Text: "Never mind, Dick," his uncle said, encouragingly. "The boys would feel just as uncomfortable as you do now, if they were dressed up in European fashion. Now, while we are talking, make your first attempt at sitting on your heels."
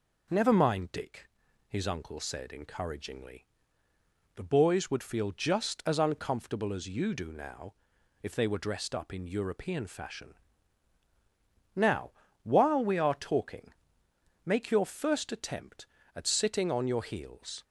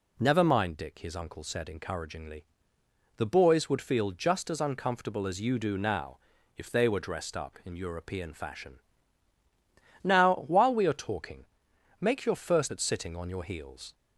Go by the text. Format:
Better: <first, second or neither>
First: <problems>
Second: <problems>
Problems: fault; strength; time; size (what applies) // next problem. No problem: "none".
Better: first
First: none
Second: skips "attempt"; at 12.7 s